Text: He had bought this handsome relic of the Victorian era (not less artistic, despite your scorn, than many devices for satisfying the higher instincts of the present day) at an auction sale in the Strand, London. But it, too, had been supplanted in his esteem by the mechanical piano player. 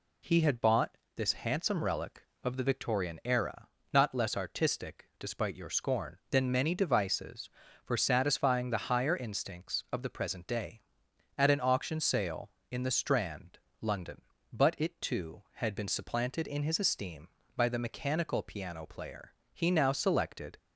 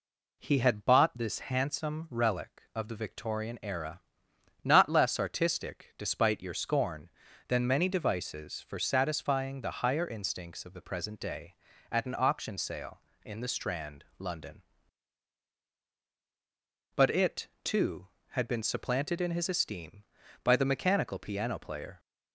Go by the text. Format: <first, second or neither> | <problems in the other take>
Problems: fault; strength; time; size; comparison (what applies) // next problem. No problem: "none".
second | pauses between "bought" and "this"; slight; at 0.9 s; 0.20 s long // goes on to say "He now selected"; noticeable; from 19.5 s on; 1.0 s long